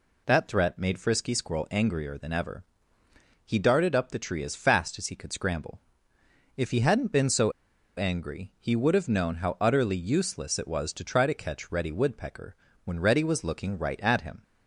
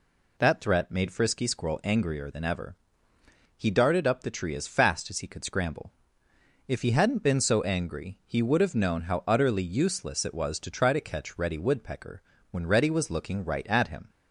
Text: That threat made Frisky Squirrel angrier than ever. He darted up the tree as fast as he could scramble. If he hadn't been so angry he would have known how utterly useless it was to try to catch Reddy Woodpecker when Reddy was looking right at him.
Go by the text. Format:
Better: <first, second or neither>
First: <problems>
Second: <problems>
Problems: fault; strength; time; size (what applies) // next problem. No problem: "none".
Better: second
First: pauses between "so" and "angry"; noticeable; at 7.5 s; 0.46 s long // pauses between "Woodpecker" and "when"; slight; at 12.5 s; 0.30 s long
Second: pauses between "Woodpecker" and "when"; slight; at 12.2 s; 0.30 s long